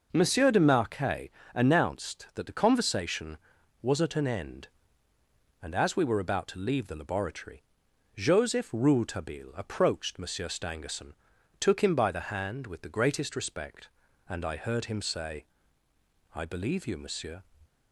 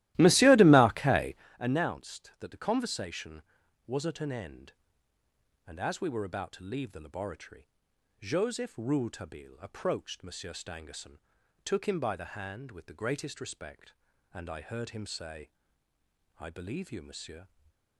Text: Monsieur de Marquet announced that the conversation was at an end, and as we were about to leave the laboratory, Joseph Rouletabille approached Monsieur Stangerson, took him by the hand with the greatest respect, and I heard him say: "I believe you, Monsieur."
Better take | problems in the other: first | starts louder than the rest; strong; until 1.5 s; 16 dB // pauses between "Marquet" and "announced"; slight; at 1.3 s; 0.24 s long; slight in the first // stays silent after the last word; slight; from 17.4 s on; 0.5 s long

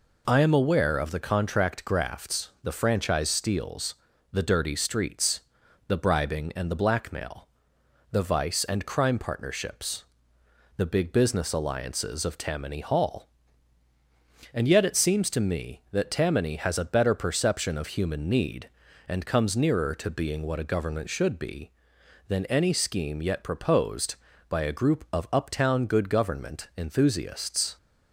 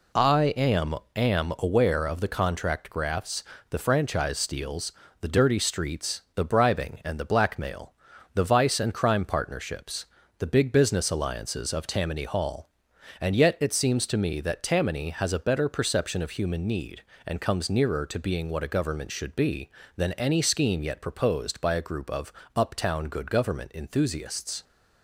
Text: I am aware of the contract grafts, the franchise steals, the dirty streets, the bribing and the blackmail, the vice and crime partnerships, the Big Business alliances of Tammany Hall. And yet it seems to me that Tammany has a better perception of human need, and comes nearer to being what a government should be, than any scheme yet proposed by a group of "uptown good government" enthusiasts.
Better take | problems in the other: first | says "am" twice; at 1.1 s // pauses between "of" and "uptown"; slight; at 22.3 s; 0.20 s long

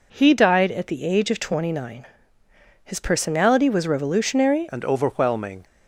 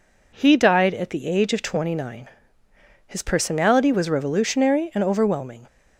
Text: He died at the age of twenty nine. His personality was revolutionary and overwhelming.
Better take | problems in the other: second | changes voice at "and"; from 4.7 s on; 0.9 s long

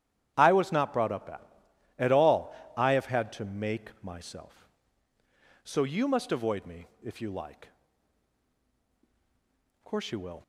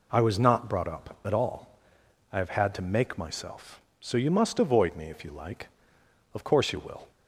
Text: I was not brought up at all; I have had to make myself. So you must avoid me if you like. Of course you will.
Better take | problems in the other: second | starts louder than the rest; strong; until 1.3 s; 11 dB // says "at" twice; at 1.9 s // pauses between "me" and "if"; slight; at 6.8 s; 0.16 s long

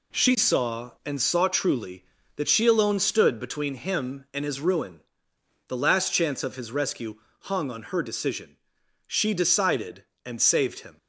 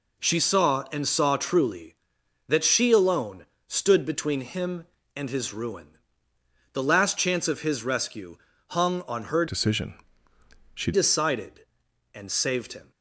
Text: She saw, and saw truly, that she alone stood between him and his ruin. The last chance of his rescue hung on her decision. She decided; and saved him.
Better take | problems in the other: first | pauses between "alone" and "stood"; slight; at 3.4 s; 0.22 s long // pauses between "rescue" and "hung"; slight; at 8.3 s; 0.32 s long; slight in the first // changes voice from "decision" to "She"; from 9.4 to 10.9 s; 1.5 s long

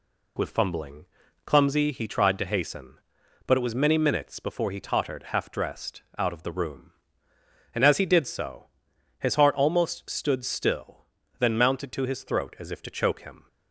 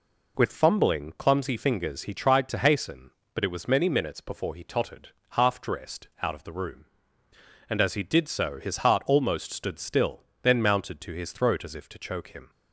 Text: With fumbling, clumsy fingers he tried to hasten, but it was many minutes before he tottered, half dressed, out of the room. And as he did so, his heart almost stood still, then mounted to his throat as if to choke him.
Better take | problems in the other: second | skips "fingers"; at 1.9 s

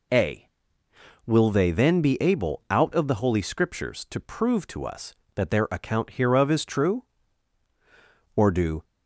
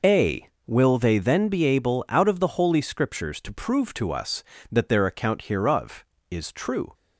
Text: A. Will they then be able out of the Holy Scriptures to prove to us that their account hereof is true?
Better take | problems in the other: second | goes on to say "or do"; slight; from 8.3 s on; 0.48 s long

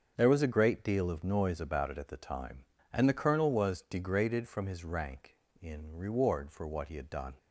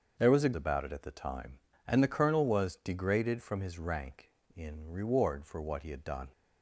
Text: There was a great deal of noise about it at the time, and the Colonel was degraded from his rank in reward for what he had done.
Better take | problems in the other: first | starts louder than the rest; until 1.1 s; 6.5 dB; also in the first // skips "great deal of noise"; at 0.5 s

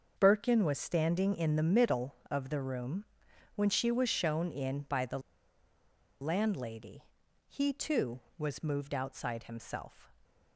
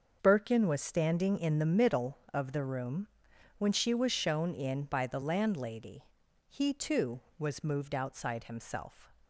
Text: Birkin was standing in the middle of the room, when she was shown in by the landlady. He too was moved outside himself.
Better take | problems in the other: second | starts louder than the rest; until 1.1 s; 6.5 dB; also in the second // pauses between "the" and "landlady"; at 5.1 s; 1.0 s long

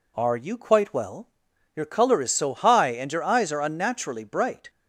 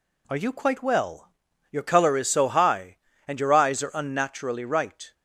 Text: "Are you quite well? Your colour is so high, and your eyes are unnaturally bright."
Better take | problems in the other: first | says "right" for "bright"; at 4.6 s

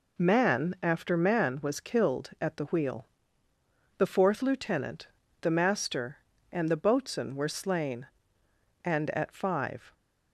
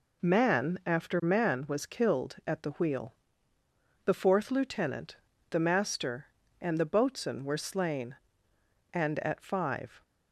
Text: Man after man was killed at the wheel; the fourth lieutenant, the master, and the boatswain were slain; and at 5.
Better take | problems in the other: neither | none

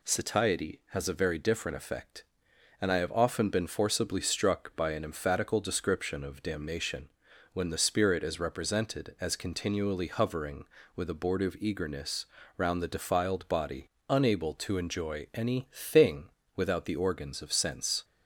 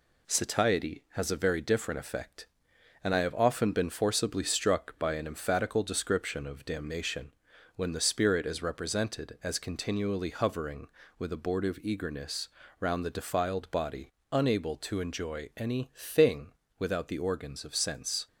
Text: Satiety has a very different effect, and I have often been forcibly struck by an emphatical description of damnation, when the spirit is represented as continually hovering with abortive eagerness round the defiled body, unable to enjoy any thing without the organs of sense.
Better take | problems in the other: first | gets quieter; slight; throughout; 3.5 dB // pauses between "eagerness" and "round"; slight; at 12.4 s; 0.30 s long; slight in the first // pauses between "thing" and "without"; slight; at 16.5 s; 0.26 s long; slight in the first

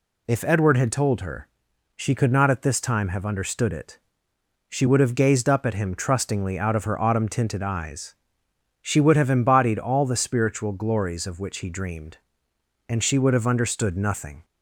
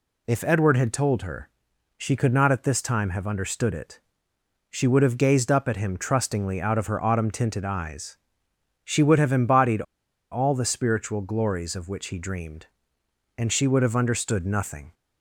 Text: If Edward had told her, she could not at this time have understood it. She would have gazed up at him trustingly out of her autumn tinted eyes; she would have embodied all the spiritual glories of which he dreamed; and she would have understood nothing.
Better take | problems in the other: first | pauses between "embodied" and "all"; noticeable; at 9.8 s; 0.48 s long

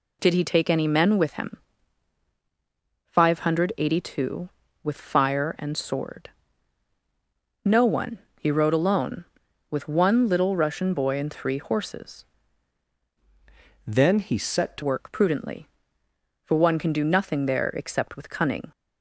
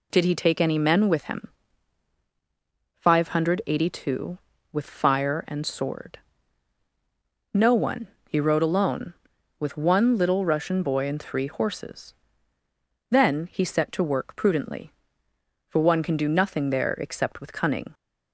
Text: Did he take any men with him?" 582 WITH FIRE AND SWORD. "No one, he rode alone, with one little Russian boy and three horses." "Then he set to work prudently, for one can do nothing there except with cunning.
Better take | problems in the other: second | changes voice from "Then" to "to"; from 13.8 to 14.8 s; 1.0 s long

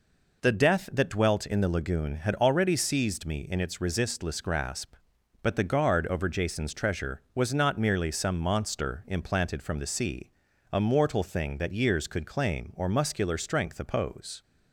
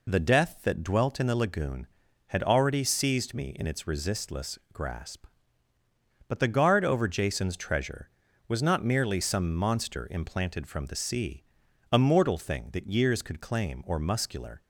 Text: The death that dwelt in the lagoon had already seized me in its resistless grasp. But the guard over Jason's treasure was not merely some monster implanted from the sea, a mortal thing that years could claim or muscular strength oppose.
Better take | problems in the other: first | stops before "strength oppose"; at 14.6 s

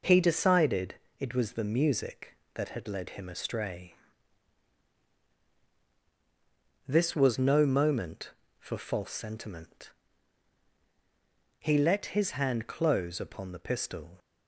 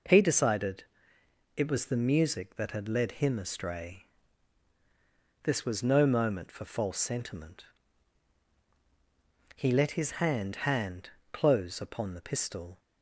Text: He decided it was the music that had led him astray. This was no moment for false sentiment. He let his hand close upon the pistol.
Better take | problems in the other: first | pauses between "decided" and "it"; noticeable; at 0.8 s; 0.72 s long; slight in the first // says "hand" twice; at 10.5 s

